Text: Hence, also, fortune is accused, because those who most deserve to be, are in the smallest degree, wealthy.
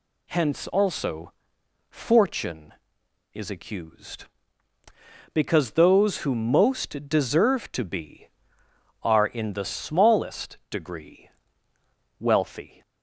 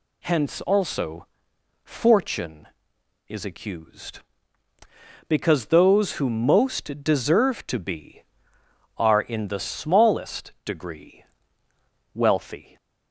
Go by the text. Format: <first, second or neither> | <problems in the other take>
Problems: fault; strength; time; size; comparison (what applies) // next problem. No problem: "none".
neither | none